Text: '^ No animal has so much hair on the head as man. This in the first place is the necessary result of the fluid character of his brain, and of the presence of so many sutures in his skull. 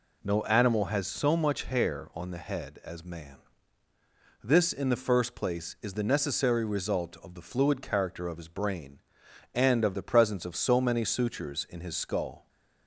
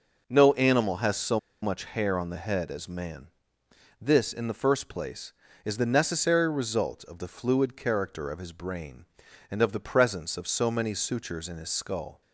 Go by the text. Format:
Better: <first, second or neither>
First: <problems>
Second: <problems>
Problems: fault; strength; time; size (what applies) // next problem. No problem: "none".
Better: first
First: none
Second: pauses between "so" and "much"; slight; at 1.3 s; 0.24 s long